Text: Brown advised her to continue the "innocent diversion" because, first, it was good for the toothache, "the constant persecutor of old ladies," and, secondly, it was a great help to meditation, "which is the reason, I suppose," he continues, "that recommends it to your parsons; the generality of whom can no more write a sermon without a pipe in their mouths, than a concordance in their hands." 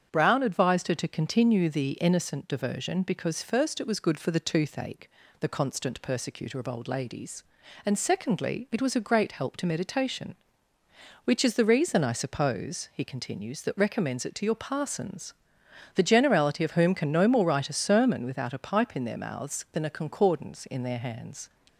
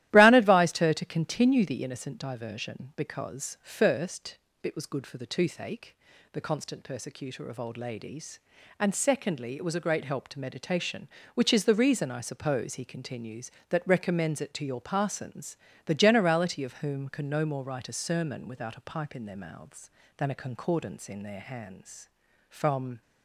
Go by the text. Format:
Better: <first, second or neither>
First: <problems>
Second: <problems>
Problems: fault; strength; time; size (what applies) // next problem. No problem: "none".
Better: first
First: starts louder than the rest; strong; until 1.1 s; 8 dB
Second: starts louder than the rest; strong; until 1.1 s; 14 dB // goes on to say "From"; from 22.4 s on; 0.52 s long